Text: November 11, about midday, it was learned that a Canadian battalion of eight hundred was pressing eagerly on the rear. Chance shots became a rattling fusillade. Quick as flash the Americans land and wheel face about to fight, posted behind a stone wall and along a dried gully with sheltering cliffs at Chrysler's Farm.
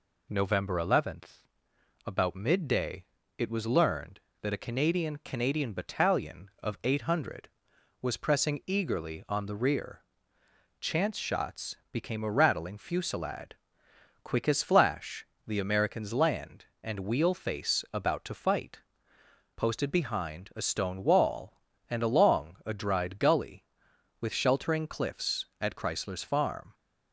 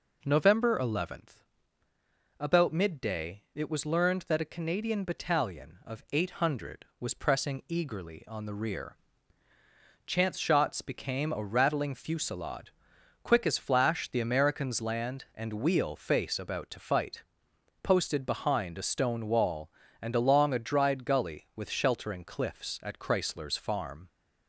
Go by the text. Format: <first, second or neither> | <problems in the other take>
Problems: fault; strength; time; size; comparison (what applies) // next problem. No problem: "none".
second | says "Canadian" twice; at 5.1 s // pauses between "shots" and "became"; slight; at 11.7 s; 0.16 s long // pauses between "flash" and "the"; slight; at 15.2 s; 0.20 s long